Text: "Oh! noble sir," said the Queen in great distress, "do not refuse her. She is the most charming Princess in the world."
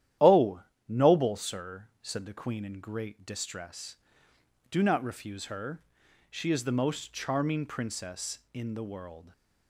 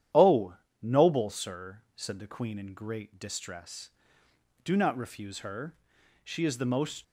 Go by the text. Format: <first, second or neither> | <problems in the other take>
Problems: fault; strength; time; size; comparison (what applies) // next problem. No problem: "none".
first | starts louder than the rest; strong; until 1.3 s; 10.5 dB; strong in the first // stops before "charming Princess in the world"; at 7.0 s